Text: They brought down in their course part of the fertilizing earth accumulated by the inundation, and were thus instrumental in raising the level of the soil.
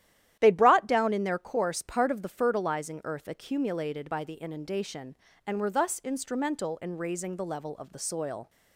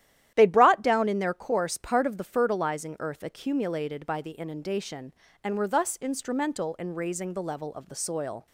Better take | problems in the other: neither | starts louder than the rest; strong; the same in both

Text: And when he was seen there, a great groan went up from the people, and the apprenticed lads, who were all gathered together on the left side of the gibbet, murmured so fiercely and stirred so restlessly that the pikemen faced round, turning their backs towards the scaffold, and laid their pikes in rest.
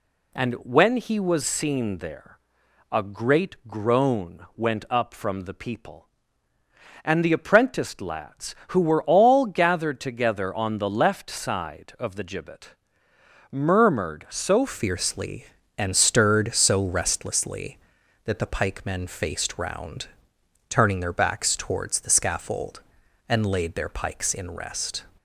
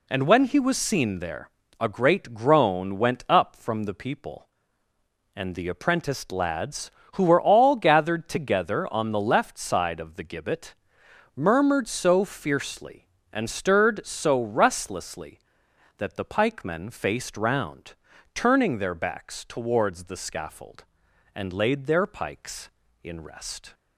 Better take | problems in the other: second | changes voice at "fiercely"; from 14.6 s on; 10.4 s long

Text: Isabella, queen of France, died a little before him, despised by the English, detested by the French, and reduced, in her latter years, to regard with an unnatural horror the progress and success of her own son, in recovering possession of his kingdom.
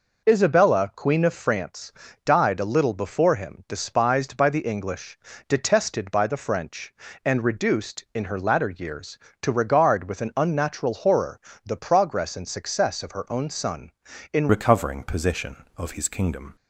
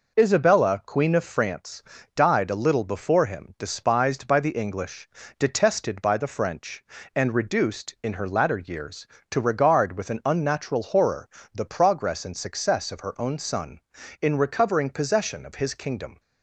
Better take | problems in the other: second | pauses between "horror" and "the"; slight; at 11.4 s; 0.24 s long; slight in the second // changes voice at "recovering"; from 14.4 s on; 2.1 s long

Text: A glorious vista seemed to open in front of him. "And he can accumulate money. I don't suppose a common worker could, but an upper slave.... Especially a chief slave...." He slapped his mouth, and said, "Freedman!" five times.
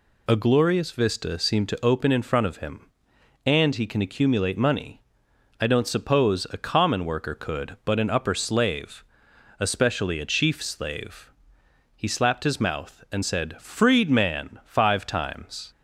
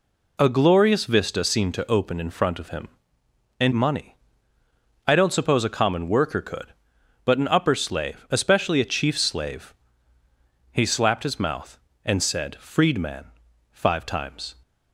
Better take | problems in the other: first | skips "he can accumulate"; at 3.7 s

